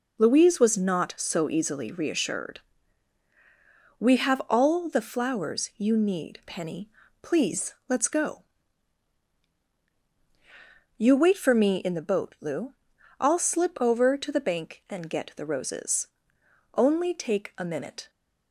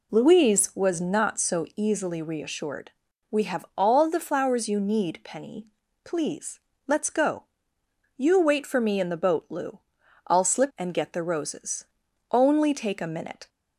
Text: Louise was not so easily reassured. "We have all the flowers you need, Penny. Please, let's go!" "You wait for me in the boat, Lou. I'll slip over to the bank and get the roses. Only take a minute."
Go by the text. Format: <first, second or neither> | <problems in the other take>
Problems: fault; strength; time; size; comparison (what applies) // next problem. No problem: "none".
first | skips "over to the bank"; at 10.7 s